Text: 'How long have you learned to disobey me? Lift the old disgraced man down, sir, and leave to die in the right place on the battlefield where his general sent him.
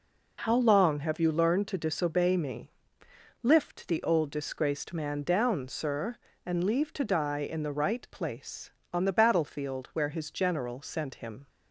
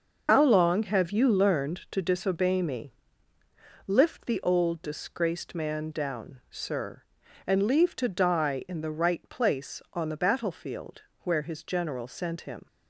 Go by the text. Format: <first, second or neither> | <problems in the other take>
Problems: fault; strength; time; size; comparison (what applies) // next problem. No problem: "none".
first | loses the start of "How"; at 0.2 s; 95 ms // starts louder than the rest; noticeable; until 1.2 s; 6 dB // pauses between "battlefield" and "where"; slight; at 11.0 s; 0.20 s long